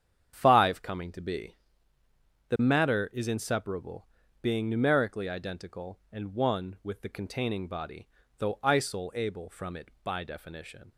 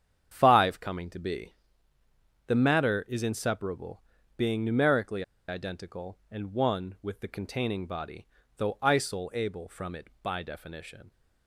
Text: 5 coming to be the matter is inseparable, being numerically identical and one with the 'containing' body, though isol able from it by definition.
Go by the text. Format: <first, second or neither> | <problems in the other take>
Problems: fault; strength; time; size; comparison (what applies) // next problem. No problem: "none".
first | starts louder than the rest; strong; until 1.3 s; 8 dB; strong in the first // pauses between "be" and "the"; noticeable; at 1.5 s; 0.92 s long; noticeable in the first // pauses between "numerically" and "identical"; slight; at 5.2 s; 0.26 s long